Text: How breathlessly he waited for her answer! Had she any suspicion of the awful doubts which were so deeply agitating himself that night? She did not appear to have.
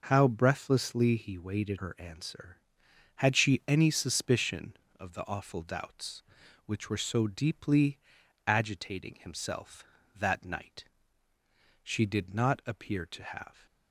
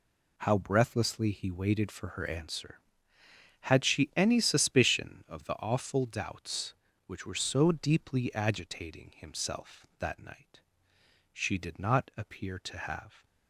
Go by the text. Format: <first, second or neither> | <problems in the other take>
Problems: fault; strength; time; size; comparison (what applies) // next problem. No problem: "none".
second | skips "for"; at 1.7 s // pauses between "deeply" and "agitating"; noticeable; at 7.9 s; 0.50 s long